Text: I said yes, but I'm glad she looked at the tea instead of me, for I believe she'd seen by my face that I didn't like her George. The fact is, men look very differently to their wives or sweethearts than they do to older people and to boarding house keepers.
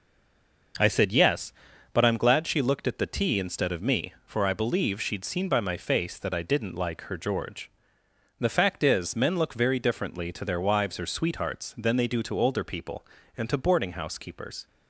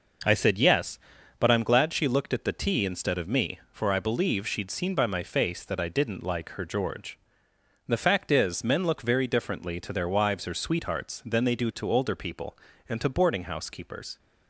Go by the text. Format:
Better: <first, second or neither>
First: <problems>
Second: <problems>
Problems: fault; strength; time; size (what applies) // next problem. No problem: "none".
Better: second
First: stays silent before the first word; slight; until 0.7 s; 0.7 s long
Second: none